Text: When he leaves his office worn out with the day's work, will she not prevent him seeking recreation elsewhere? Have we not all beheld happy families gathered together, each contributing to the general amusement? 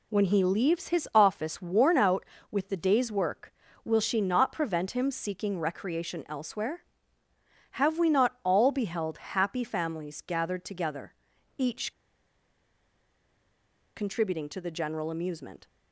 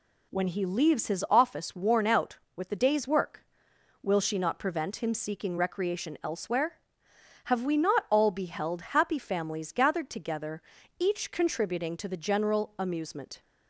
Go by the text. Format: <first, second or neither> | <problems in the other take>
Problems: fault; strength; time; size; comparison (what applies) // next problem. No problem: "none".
second | pauses between "each" and "contributing"; strong; at 11.9 s; 2.0 s long